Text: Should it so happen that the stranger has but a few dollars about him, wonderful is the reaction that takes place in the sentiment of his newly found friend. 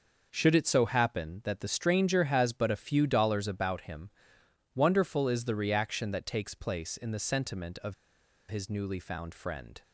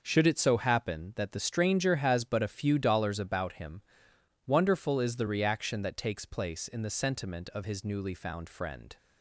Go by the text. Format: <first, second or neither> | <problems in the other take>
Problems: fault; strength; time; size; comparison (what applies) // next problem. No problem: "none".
second | pauses between "of" and "his"; noticeable; at 7.9 s; 0.55 s long